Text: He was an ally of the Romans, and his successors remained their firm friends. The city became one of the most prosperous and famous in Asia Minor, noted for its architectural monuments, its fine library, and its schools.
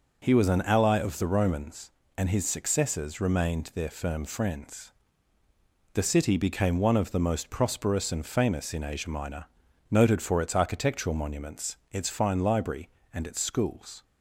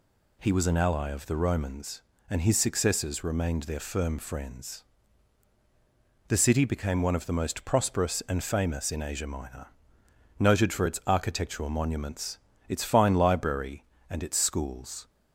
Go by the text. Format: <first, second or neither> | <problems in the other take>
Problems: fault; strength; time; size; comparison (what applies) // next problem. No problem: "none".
neither | none